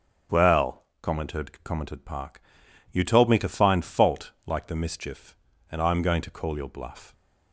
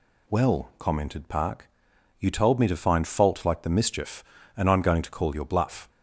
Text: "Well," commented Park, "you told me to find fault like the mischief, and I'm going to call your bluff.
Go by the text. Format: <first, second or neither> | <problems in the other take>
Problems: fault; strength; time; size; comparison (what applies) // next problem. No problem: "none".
second | starts louder than the rest; until 1.4 s; 6.5 dB // says "commented" twice; at 1.6 s // pauses between "fault" and "like"; slight; at 4.3 s; 0.16 s long